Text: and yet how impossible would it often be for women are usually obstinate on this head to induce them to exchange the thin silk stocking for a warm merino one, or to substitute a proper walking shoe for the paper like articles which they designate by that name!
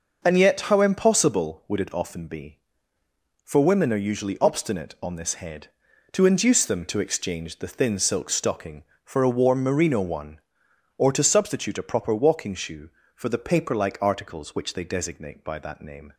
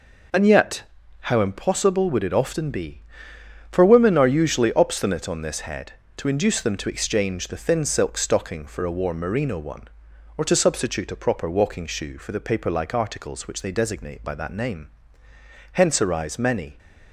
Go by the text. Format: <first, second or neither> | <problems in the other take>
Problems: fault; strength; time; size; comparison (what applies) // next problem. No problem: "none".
first | pauses between "yet" and "how"; at 0.8 s; 0.40 s long // goes on to say "Hence arise many"; noticeable; from 15.7 s on; 1.0 s long